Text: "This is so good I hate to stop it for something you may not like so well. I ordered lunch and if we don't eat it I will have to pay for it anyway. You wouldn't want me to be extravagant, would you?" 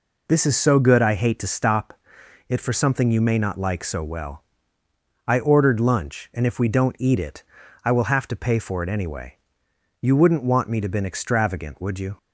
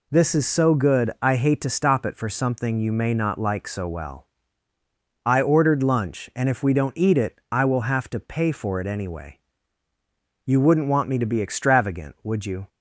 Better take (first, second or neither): second